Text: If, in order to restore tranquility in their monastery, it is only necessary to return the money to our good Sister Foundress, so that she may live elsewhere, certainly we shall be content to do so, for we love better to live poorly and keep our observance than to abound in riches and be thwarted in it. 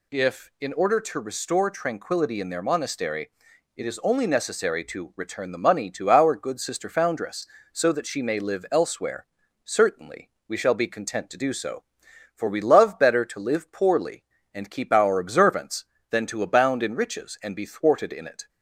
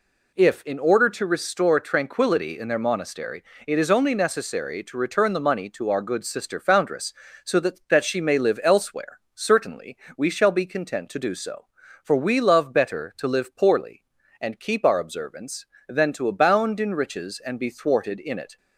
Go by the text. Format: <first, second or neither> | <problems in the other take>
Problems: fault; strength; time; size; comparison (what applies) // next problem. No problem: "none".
first | says "that" twice; at 7.8 s // pauses between "certainly" and "we"; slight; at 9.9 s; 0.22 s long; slight in the first